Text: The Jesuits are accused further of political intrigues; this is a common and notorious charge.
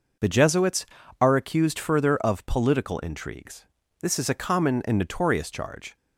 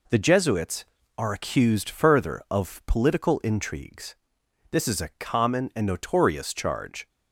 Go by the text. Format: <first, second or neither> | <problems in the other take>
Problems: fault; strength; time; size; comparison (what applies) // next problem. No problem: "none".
neither | none